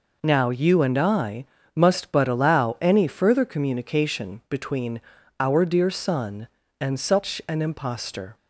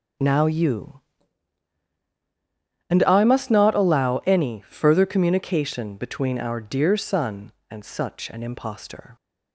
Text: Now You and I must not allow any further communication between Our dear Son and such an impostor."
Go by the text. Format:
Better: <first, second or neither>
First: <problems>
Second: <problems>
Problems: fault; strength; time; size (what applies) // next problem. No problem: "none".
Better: second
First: pauses between "I" and "must"; slight; at 1.4 s; 0.28 s long // says "but" for "not"; at 2.1 s // pauses between "between" and "Our"; at 4.9 s; 0.38 s long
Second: none